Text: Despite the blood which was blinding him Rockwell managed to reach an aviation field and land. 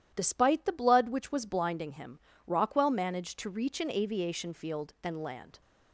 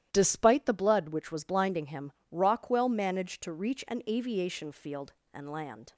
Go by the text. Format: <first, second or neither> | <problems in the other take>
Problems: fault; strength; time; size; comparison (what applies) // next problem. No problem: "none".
neither | starts louder than the rest; strong; the same in both // pauses between "him" and "Rockwell"; slight; the same in both